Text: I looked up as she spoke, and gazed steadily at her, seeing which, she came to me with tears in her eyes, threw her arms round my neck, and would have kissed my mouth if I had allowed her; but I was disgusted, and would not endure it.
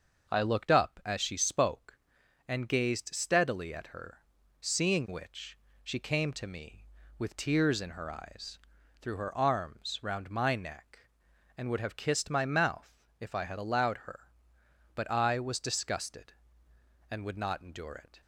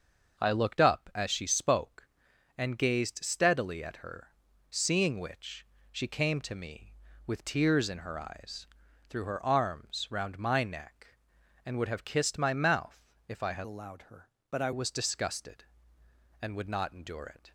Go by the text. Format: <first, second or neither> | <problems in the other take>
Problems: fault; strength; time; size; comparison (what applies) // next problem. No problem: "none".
first | starts louder than the rest; until 1.4 s; 6.5 dB; also in the first // pauses between "mouth" and "if"; slight; at 13.0 s; 0.26 s long; slight in the first // changes voice from "allowed" to "I"; from 13.6 to 14.7 s; 1.1 s long